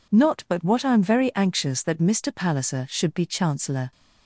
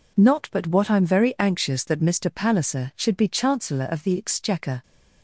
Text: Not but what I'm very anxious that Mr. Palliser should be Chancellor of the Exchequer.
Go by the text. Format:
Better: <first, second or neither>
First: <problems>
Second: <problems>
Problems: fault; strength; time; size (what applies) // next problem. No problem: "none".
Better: second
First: stops before "of the Exchequer"; at 3.9 s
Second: none